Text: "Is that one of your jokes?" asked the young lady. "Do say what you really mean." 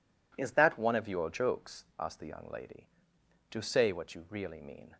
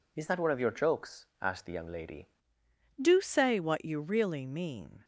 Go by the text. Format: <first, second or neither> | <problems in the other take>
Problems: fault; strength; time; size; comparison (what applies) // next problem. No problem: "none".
first | changes voice at "Do"; from 2.9 s on; 2.1 s long